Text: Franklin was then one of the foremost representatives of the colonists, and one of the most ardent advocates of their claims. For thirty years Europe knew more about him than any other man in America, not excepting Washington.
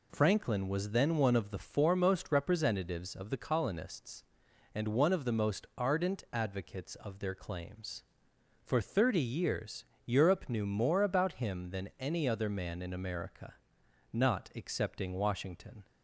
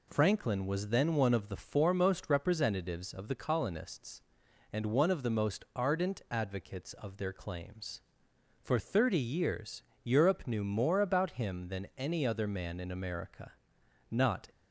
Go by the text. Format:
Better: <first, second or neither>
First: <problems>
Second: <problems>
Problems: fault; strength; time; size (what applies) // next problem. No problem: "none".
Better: first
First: pauses between "years" and "Europe"; slight; at 9.8 s; 0.20 s long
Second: pauses between "years" and "Europe"; slight; at 9.8 s; 0.20 s long // stops before "excepting Washington"; at 14.4 s